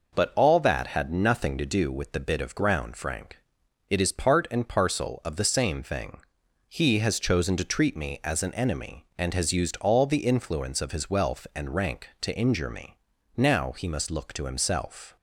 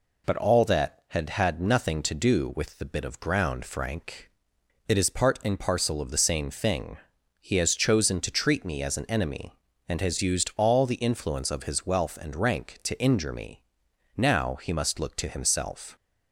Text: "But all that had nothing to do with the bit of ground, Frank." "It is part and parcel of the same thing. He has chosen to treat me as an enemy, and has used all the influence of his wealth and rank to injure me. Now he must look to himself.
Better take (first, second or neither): first